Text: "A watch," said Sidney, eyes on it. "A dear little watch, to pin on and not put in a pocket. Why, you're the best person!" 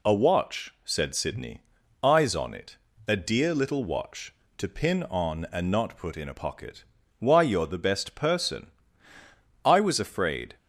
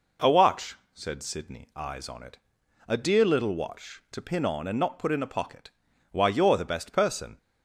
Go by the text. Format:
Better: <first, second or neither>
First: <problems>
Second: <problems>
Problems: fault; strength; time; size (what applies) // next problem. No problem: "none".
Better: second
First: goes on to say "I was afraid"; noticeable; from 9.6 s on; 0.92 s long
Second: none